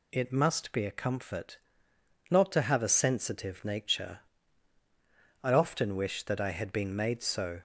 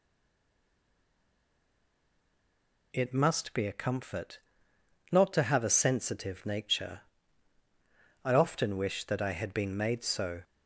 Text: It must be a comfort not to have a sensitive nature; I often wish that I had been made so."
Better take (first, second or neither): first